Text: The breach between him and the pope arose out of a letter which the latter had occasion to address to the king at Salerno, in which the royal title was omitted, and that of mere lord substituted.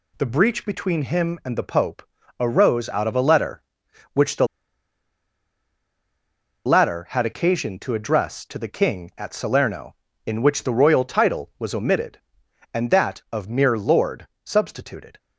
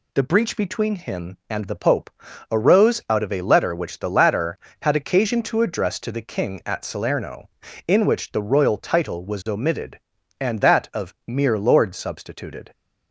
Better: second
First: pauses between "pope" and "arose"; slight; at 2.0 s; 0.36 s long // pauses between "the" and "latter"; strong; at 4.4 s; 2.1 s long // pauses between "lord" and "substituted"; slight; at 14.2 s; 0.18 s long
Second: pauses between "pope" and "arose"; at 2.0 s; 0.42 s long

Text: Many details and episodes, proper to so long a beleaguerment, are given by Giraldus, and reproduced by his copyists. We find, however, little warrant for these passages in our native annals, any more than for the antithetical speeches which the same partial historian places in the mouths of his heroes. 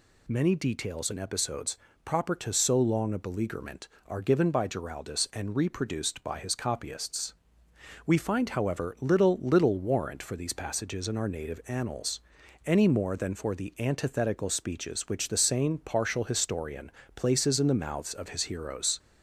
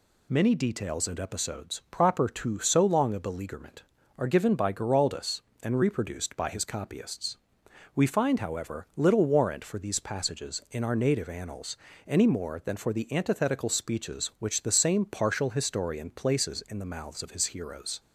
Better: second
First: says "little" twice; at 9.4 s // pauses between "historian" and "places"; slight; at 16.9 s; 0.24 s long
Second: none

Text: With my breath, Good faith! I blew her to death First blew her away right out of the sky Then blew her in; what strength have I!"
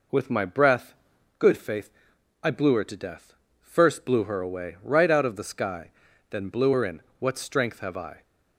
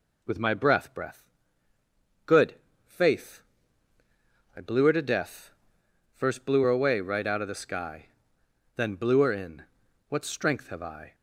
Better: first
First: pauses between "death" and "First"; slight; at 3.3 s; 0.26 s long // pauses between "sky" and "Then"; at 5.9 s; 0.40 s long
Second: says "breath" twice; at 0.9 s // pauses between "Good" and "faith"; slight; at 2.5 s; 0.32 s long // pauses between "death" and "First"; noticeable; at 5.4 s; 0.64 s long // pauses between "sky" and "Then"; noticeable; at 8.0 s; 0.66 s long

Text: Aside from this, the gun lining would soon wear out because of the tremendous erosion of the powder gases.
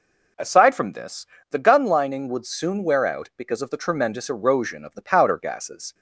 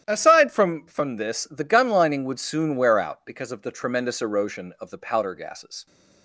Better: first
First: none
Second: starts louder than the rest; strong; until 1.0 s; 11.5 dB // says "from" twice; at 0.8 s

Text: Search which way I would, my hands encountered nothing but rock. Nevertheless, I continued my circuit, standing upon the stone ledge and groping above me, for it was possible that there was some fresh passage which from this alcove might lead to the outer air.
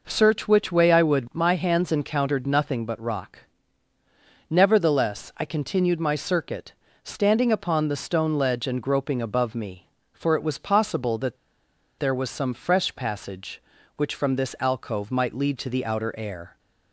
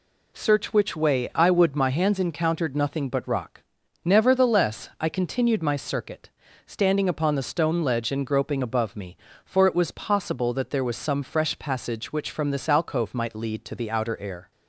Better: second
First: pauses between "that" and "there"; noticeable; at 11.3 s; 0.63 s long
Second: none

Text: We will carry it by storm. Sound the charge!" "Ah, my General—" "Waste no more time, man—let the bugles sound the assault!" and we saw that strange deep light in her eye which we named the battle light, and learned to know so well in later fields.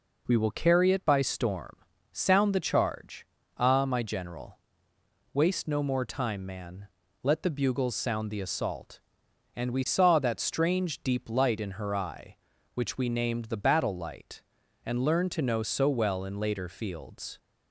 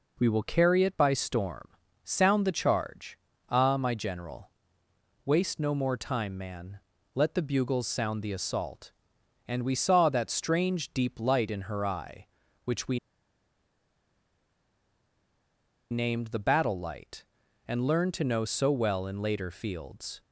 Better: first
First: none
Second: pauses between "we" and "named"; strong; at 12.9 s; 2.9 s long

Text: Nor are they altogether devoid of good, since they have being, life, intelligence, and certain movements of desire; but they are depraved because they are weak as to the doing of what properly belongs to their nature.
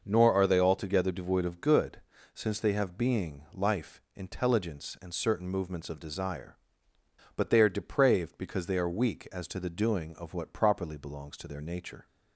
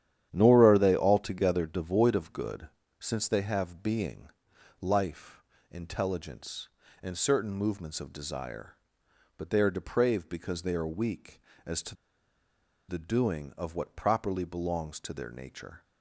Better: first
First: none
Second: starts louder than the rest; strong; until 1.3 s; 10 dB // pauses between "to" and "the"; noticeable; at 11.9 s; 0.93 s long

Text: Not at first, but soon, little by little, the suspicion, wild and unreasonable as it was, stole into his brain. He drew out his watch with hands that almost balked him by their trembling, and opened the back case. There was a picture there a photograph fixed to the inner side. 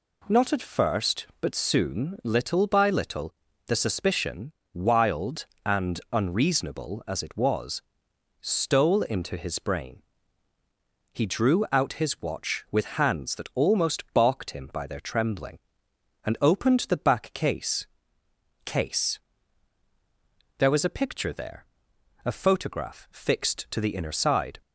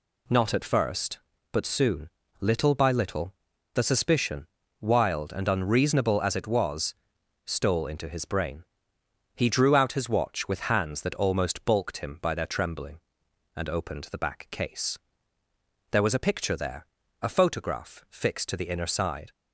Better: second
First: says "case" twice; at 18.6 s // pauses between "there" and "a"; noticeable; at 21.6 s; 0.60 s long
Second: pauses between "there" and "a"; at 16.8 s; 0.38 s long

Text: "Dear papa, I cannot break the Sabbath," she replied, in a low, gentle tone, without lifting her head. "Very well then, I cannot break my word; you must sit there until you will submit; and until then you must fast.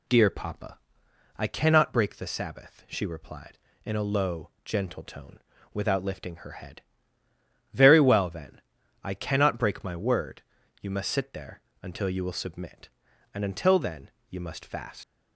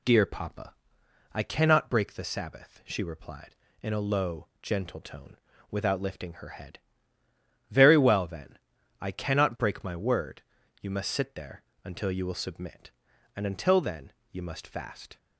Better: second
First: pauses between "there" and "until"; slight; at 11.6 s; 0.20 s long // pauses between "then" and "you"; slight; at 14.1 s; 0.18 s long // leaves "fast" unfinished; at 15.0 s; 115 ms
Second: pauses between "there" and "until"; slight; at 11.6 s; 0.20 s long // pauses between "then" and "you"; slight; at 14.1 s; 0.18 s long

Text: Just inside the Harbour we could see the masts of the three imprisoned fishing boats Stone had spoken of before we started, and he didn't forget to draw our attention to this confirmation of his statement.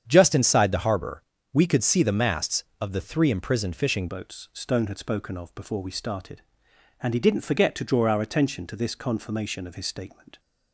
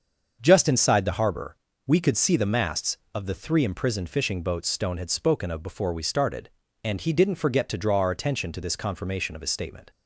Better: second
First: starts louder than the rest; strong; until 1.0 s; 8 dB // pauses between "Harbour" and "we"; slight; at 1.2 s; 0.28 s long // changes voice at "boats"; from 4.0 s on; 6.3 s long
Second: starts louder than the rest; until 1.4 s; 6.5 dB // pauses between "Harbour" and "we"; slight; at 1.5 s; 0.28 s long

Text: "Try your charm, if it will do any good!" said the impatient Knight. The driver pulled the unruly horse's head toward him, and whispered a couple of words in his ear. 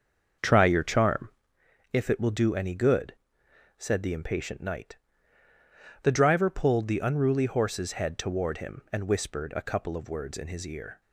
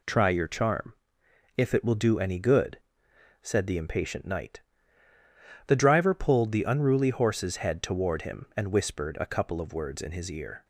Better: second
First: starts louder than the rest; until 1.5 s; 6.5 dB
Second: none

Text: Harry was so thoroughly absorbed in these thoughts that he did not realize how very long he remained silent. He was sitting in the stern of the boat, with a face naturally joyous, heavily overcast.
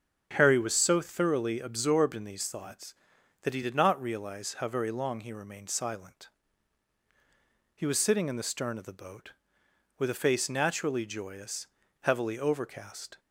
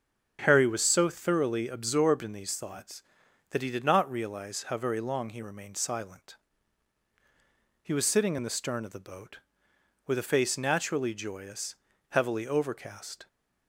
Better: neither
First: starts louder than the rest; until 1.3 s; 7 dB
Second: starts louder than the rest; until 1.4 s; 6.5 dB

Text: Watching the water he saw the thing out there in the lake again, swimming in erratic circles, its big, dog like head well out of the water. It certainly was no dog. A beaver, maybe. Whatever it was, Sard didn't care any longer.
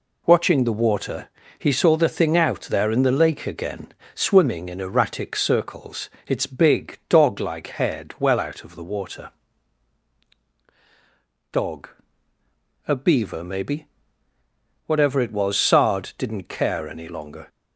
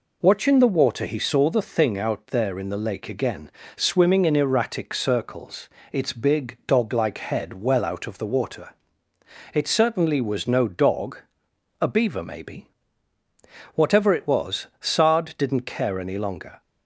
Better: second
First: pauses between "water" and "he"; slight; at 1.2 s; 0.30 s long // skips "It certainly was no"; at 10.4 s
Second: none

